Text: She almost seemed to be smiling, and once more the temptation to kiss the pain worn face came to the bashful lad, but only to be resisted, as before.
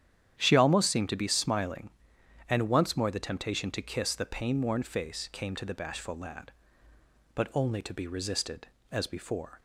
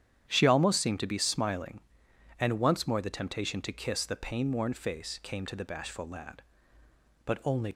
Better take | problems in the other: first | starts louder than the rest; strong; until 1.2 s; 9.5 dB; strong in the first // stops before "to be resisted as before"; at 7.7 s

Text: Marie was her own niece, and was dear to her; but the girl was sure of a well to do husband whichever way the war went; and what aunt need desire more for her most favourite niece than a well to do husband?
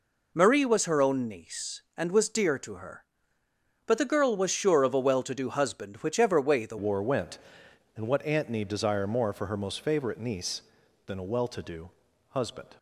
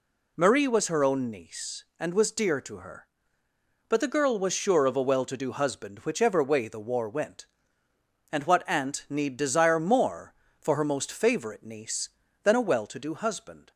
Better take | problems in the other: second | changes voice at "war"; from 6.7 s on; 6.0 s long // pauses between "do" and "husband"; at 11.8 s; 0.38 s long

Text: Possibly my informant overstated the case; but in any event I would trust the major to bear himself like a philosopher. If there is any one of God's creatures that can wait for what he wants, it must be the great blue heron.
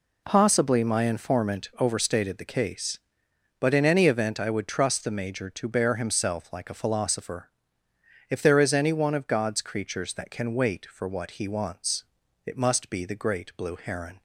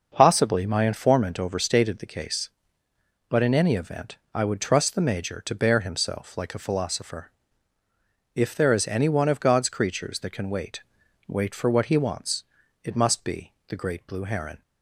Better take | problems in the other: first | starts louder than the rest; noticeable; until 1.1 s; 6 dB // pauses between "event" and "I"; slight; at 4.1 s; 0.18 s long // says "wait" twice; at 11.2 s // pauses between "be" and "the"; slight; at 13.5 s; 0.16 s long

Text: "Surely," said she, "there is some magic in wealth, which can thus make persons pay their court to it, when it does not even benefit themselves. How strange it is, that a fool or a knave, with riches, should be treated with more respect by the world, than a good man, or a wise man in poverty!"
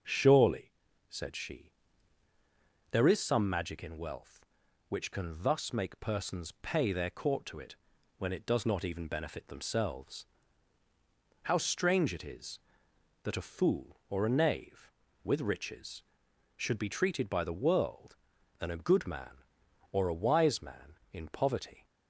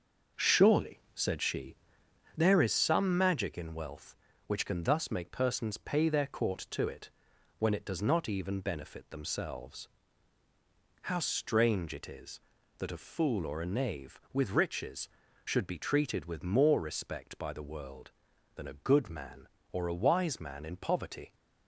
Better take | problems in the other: second | starts louder than the rest; until 1.4 s; 6.5 dB; also in the second // skips "with more respect"; at 17.2 s

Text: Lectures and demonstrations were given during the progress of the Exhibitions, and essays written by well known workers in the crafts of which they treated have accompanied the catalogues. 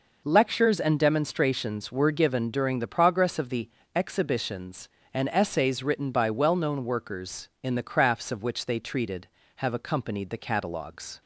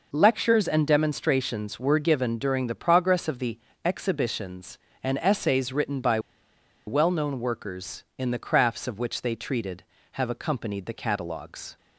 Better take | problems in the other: first | pauses between "the" and "Exhibitions"; slight; at 3.5 s; 0.26 s long; slight in the first // pauses between "by" and "well"; noticeable; at 6.1 s; 0.68 s long

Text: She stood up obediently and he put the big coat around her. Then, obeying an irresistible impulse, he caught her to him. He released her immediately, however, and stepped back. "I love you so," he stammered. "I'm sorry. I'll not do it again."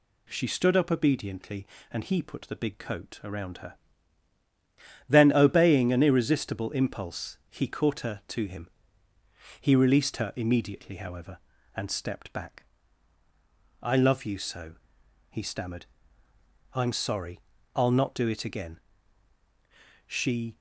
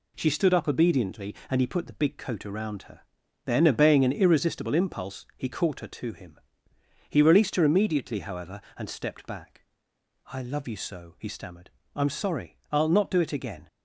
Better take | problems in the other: second | goes on to say "She"; from 20.0 s on; 0.52 s long

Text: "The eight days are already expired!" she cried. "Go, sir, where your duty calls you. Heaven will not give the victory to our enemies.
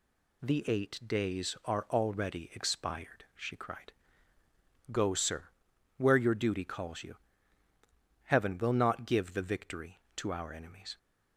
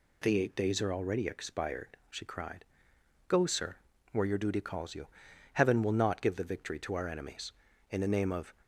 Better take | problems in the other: first | goes on to say "In the name of"; noticeable; from 7.9 s on; 0.64 s long

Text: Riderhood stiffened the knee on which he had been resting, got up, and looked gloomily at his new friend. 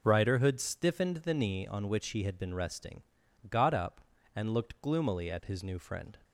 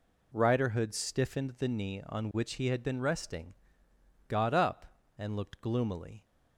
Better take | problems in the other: first | stops before "at his new friend"; at 6.2 s

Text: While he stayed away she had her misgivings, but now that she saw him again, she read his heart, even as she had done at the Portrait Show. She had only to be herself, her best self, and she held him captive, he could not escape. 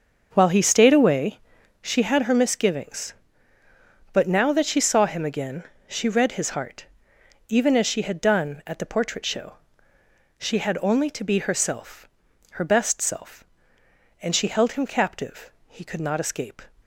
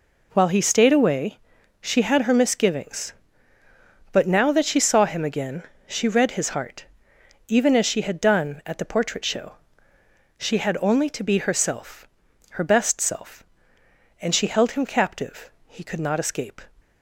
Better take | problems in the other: second | starts louder than the rest; until 1.9 s; 6.5 dB // pauses between "away" and "she"; at 1.3 s; 0.42 s long; also in the second

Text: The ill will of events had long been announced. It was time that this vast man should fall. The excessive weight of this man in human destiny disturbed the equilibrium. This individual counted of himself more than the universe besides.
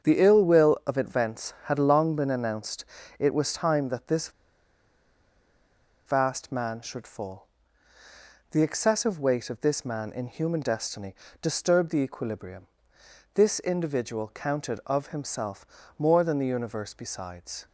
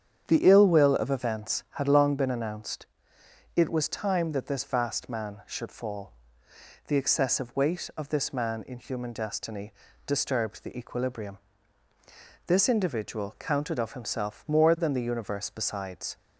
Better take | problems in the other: second | starts louder than the rest; strong; until 1.1 s; 7.5 dB; strong in the second // pauses between "this" and "vast"; strong; at 4.2 s; 1.7 s long // pauses between "destiny" and "disturbed"; slight; at 11.1 s; 0.26 s long; slight in the second // pauses between "himself" and "more"; slight; at 15.6 s; 0.32 s long

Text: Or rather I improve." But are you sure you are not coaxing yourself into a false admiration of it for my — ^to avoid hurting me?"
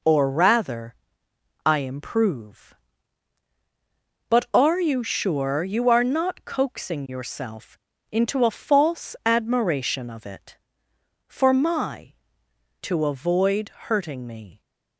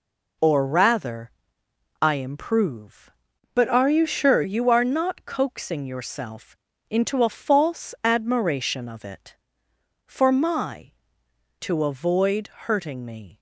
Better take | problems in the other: first | pauses between "rather" and "I"; noticeable; at 1.3 s; 0.70 s long; noticeable in the first // changes voice from "But" to "sure"; from 3.5 to 4.4 s; 0.9 s long // pauses between "yourself" and "into"; slight; at 6.5 s; 0.32 s long; slight in the first // pauses between "avoid" and "hurting"; slight; at 12.4 s; 0.18 s long; slight in the first

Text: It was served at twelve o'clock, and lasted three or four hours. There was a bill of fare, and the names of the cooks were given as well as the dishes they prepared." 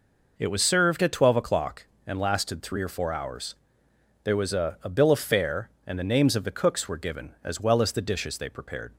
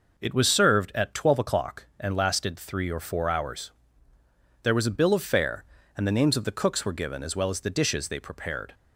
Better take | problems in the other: second | says "a" twice; at 4.8 s

